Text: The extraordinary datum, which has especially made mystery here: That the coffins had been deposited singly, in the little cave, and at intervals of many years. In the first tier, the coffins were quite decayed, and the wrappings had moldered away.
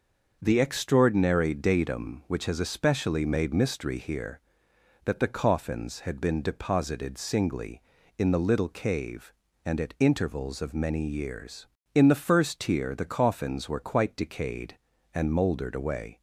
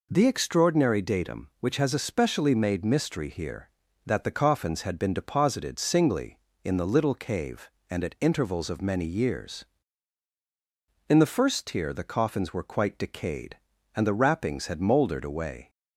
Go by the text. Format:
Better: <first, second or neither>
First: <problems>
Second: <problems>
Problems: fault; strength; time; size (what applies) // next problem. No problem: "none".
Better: second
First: starts louder than the rest; noticeable; until 1.4 s; 6 dB // skips "the wrappings had"; at 15.3 s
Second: none